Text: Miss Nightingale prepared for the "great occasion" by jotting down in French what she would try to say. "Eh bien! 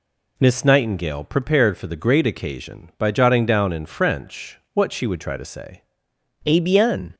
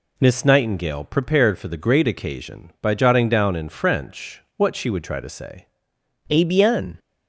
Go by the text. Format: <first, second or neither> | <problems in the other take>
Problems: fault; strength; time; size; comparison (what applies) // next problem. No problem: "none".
neither | pauses between "French" and "what"; slight; the same in both